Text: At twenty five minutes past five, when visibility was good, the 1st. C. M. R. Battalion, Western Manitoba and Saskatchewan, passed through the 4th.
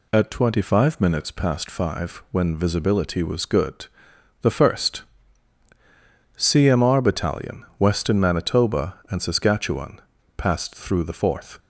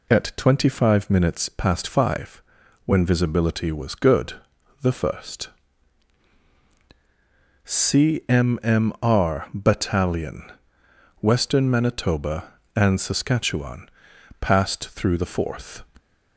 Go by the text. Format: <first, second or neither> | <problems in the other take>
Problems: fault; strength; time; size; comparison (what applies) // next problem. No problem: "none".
first | says "M" twice; at 8.6 s